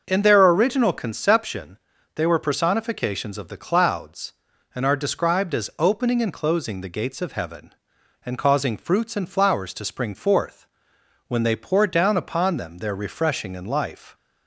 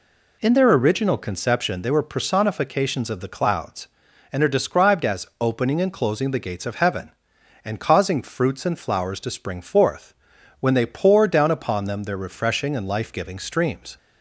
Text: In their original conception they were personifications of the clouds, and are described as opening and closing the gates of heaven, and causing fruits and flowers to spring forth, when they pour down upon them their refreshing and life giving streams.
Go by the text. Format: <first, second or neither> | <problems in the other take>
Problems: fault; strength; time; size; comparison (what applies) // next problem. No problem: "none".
second | starts louder than the rest; until 1.0 s; 6.5 dB // pauses between "conception" and "they"; slight; at 1.7 s; 0.34 s long // stops before "giving streams"; at 14.1 s